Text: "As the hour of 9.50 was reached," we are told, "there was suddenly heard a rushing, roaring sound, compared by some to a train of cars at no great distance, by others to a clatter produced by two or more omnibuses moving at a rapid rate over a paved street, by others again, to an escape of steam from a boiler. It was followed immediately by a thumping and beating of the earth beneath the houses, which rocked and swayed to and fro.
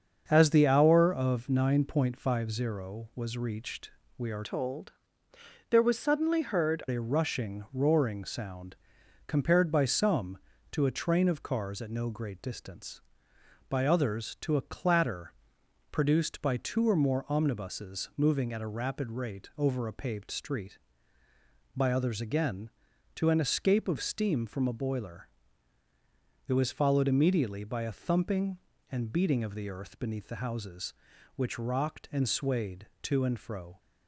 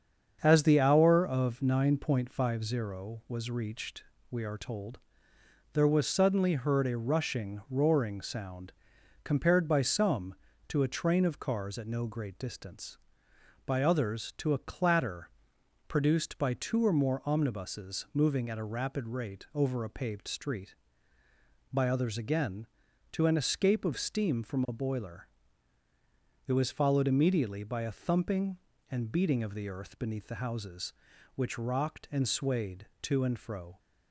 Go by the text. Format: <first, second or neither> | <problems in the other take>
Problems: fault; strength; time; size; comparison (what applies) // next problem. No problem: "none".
second | starts louder than the rest; until 1.2 s; 6.5 dB; also in the second // changes voice from "told" to "heard"; from 4.4 to 6.8 s; 2.4 s long // pauses between "clatter" and "produced"; noticeable; at 15.3 s; 0.62 s long; noticeable in the second